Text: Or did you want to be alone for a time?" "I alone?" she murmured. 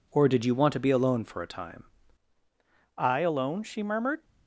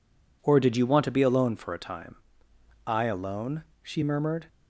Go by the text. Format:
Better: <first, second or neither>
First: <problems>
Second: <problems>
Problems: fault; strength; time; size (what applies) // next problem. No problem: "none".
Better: second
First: changes voice at "I"; from 2.9 s on; 1.3 s long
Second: none